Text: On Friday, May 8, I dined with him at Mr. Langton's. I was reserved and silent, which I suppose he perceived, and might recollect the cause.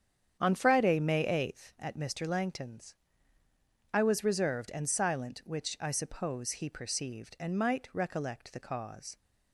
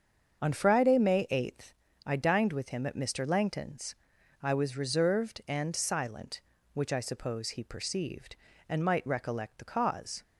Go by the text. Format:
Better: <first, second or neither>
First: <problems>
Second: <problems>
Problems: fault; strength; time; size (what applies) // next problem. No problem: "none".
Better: second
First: starts louder than the rest; strong; until 1.4 s; 8.5 dB // skips "I dined with him"; at 1.7 s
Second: starts louder than the rest; until 1.4 s; 7 dB